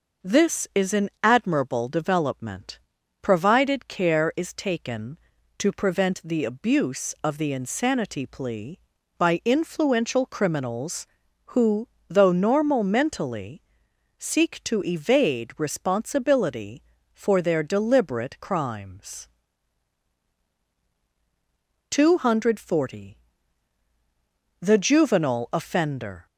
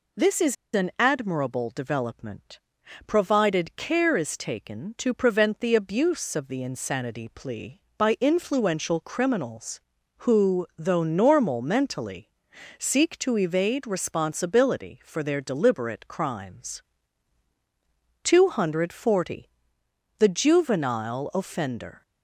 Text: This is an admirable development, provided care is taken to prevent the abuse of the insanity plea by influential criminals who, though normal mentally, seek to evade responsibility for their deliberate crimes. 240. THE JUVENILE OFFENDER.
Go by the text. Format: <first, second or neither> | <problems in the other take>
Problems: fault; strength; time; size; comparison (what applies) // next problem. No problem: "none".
first | pauses between "is" and "an"; slight; at 0.5 s; 0.20 s long